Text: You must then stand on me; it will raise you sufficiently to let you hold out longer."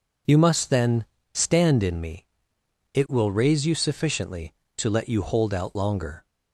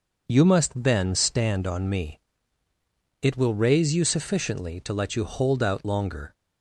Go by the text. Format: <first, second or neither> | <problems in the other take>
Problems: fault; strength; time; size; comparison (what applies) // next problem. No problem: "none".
second | pauses between "then" and "stand"; slight; at 1.0 s; 0.30 s long // says "in" for "on"; at 1.8 s